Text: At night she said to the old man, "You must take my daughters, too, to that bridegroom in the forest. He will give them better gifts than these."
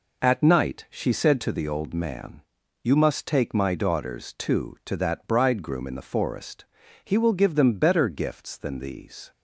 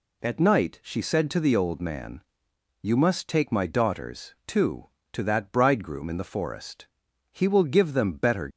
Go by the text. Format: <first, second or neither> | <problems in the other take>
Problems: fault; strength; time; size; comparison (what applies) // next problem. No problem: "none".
first | stops before "gifts than these"; at 8.4 s